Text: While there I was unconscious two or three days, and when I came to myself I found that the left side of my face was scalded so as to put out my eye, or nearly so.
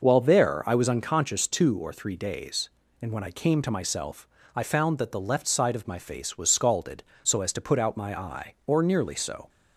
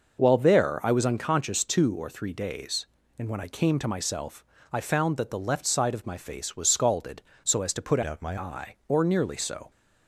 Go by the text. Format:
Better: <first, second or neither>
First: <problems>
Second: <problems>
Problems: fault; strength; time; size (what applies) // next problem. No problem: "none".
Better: first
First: pauses between "myself" and "I"; slight; at 4.2 s; 0.26 s long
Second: pauses between "myself" and "I"; slight; at 4.4 s; 0.26 s long // changes voice from "out" to "my"; from 8.0 to 8.3 s; 0.3 s long